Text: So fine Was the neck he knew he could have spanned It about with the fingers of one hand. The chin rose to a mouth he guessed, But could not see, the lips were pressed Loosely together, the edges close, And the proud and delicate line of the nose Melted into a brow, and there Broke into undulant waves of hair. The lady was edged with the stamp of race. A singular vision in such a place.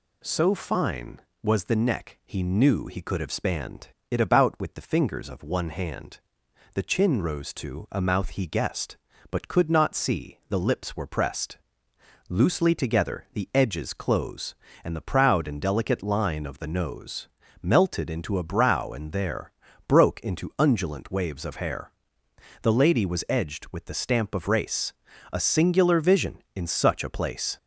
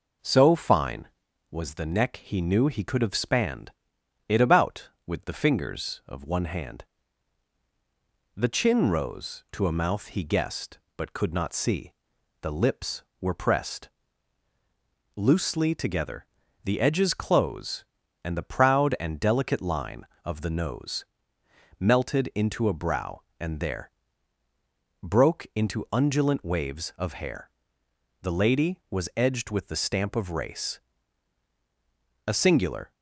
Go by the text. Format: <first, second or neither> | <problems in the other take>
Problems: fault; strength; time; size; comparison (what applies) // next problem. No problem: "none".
first | pauses between "spanned" and "It"; noticeable; at 3.7 s; 0.56 s long; slight in the first // pauses between "pressed" and "Loosely"; strong; at 13.8 s; 1.2 s long; noticeable in the first // pauses between "nose" and "Melted"; noticeable; at 21.0 s; 0.74 s long; slight in the first // pauses between "there" and "Broke"; at 23.8 s; 1.1 s long; slight in the first // stops before "vision in such a place"; at 32.9 s